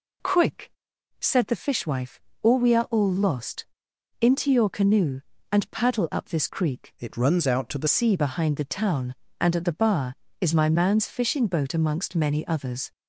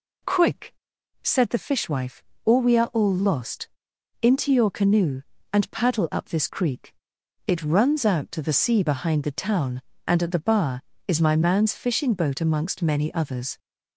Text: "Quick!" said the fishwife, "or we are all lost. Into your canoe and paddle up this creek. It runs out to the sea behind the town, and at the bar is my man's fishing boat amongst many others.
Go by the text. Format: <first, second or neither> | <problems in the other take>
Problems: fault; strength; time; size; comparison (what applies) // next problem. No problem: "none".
second | changes voice from "It" to "the"; from 6.9 to 7.8 s; 0.9 s long